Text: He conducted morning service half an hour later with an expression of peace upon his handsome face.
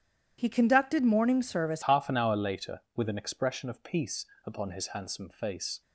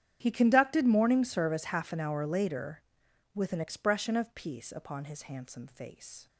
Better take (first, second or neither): second